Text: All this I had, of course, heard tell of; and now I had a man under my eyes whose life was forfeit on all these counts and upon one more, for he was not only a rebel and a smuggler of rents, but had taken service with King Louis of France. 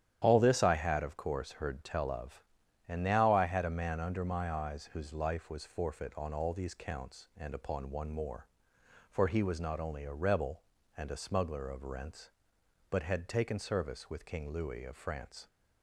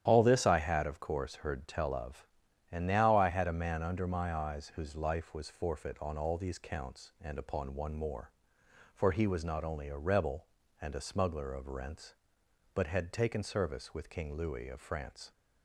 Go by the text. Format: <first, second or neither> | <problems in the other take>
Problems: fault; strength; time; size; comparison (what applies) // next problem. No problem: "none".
neither | starts louder than the rest; strong; the same in both